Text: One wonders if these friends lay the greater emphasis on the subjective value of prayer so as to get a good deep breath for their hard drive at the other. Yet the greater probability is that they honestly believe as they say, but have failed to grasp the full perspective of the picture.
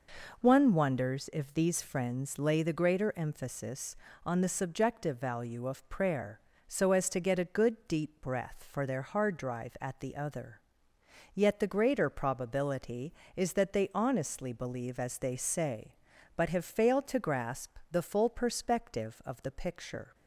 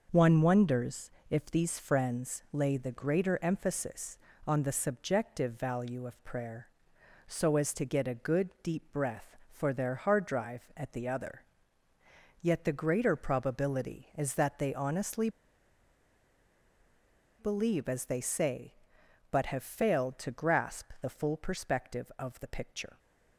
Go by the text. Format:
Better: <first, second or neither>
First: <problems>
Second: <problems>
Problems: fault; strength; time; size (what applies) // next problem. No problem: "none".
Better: first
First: none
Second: pauses between "wonders" and "if"; slight; at 1.0 s; 0.20 s long // pauses between "honestly" and "believe"; strong; at 15.2 s; 2.1 s long